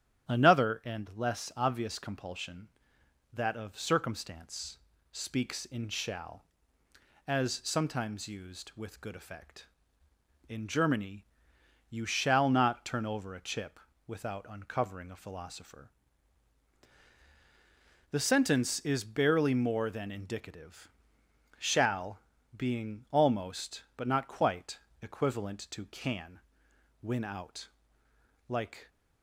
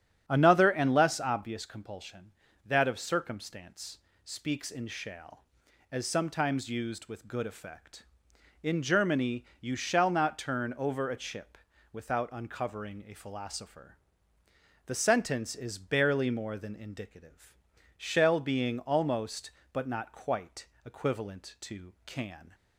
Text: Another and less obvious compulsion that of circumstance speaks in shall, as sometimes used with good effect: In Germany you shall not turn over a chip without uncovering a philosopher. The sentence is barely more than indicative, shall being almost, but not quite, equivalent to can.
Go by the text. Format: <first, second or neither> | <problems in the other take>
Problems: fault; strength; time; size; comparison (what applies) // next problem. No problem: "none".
second | starts louder than the rest; strong; until 1.3 s; 10 dB; strong in the second // pauses between "circumstance" and "speaks"; slight; at 4.7 s; 0.34 s long; slight in the second // pauses between "Germany" and "you"; noticeable; at 11.2 s; 0.64 s long; slight in the second // pauses between "chip" and "without"; slight; at 13.7 s; 0.30 s long; slight in the second // pauses between "shall" and "being"; at 22.1 s; 0.38 s long // goes on to say "Win out Like"; strong; from 27.0 s on; 1.8 s long